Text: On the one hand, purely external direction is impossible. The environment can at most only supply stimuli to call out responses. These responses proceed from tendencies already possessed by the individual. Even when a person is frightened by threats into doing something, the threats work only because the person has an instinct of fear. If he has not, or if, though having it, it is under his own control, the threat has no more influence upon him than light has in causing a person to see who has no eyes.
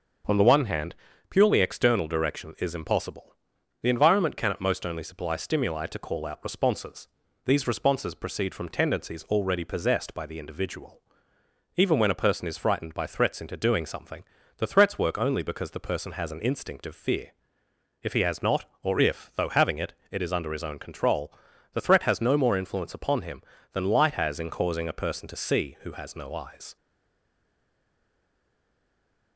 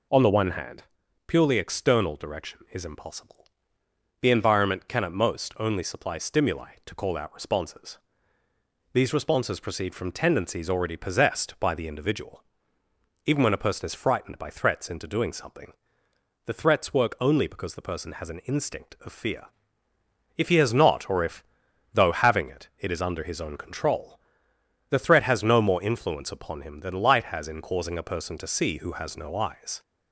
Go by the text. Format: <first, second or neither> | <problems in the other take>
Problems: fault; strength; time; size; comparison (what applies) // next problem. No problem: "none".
second | starts louder than the rest; until 1.6 s; 6.5 dB // stays silent after the last word; strong; from 26.7 s on; 2.6 s long